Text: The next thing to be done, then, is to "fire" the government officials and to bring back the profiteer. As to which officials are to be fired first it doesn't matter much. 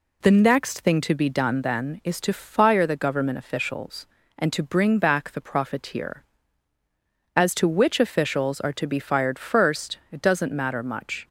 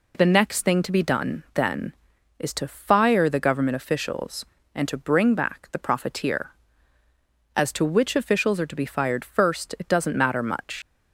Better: first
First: none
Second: leaves "much" unfinished; at 10.8 s; 75 ms

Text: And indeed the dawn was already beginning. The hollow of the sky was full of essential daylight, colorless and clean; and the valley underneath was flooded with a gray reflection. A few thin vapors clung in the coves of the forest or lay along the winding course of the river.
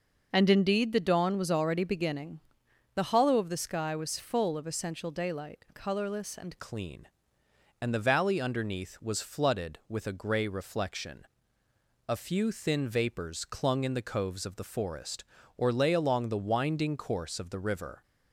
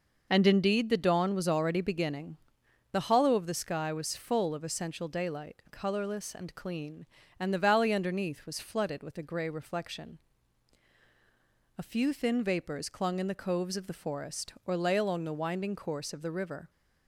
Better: second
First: changes voice at "clean"; from 6.5 s on; 11.5 s long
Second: none

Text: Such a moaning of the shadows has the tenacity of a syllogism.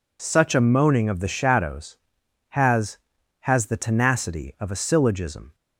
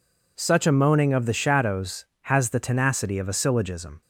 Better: second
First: says "has" twice; at 3.3 s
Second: none

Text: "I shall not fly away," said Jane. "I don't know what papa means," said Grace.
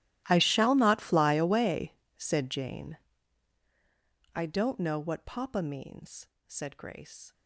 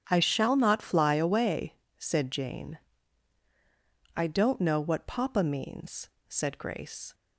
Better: second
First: gets quieter; strong; throughout; 24 dB // starts louder than the rest; strong; until 1.2 s; 15 dB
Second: starts louder than the rest; strong; until 1.1 s; 9 dB

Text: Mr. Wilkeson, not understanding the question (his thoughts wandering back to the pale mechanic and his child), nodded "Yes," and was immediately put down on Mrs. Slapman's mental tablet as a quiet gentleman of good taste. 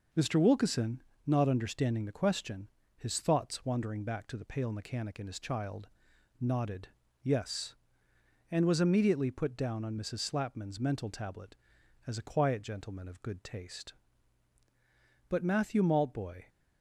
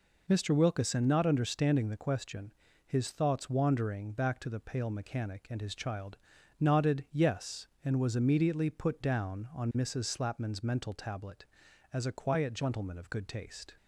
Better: second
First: pauses between "nodded" and "Yes"; slight; at 6.8 s; 0.34 s long // goes on to say "But Matthew Maltboy"; noticeable; from 15.2 s on; 1.1 s long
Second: none

